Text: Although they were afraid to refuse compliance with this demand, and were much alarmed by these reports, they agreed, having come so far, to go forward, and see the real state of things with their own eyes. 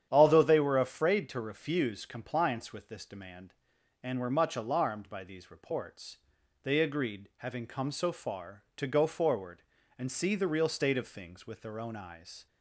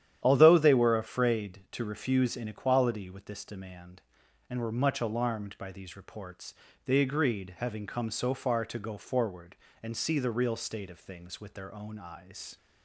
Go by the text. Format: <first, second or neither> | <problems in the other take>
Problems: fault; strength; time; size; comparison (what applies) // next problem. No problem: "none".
first | starts louder than the rest; strong; until 1.2 s; 10.5 dB; strong in the first // says "inequality" for "compliance"; at 2.3 s